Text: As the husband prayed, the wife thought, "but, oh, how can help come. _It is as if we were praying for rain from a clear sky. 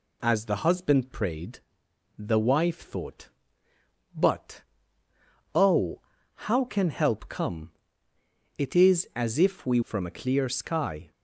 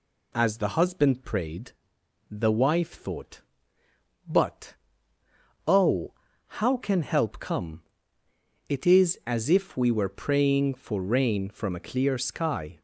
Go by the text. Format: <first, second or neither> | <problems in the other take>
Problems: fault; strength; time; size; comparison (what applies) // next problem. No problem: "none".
second | skips "were praying for rain"; at 9.8 s